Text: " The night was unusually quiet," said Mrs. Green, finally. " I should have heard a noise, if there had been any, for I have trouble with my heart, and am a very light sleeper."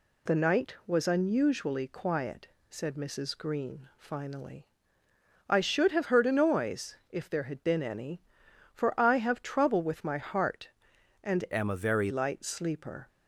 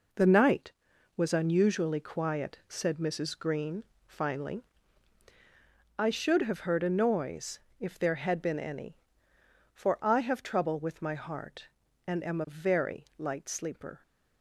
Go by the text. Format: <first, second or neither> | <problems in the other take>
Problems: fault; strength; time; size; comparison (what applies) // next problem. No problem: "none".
second | changes voice from "am" to "very"; from 11.5 to 12.1 s; 0.6 s long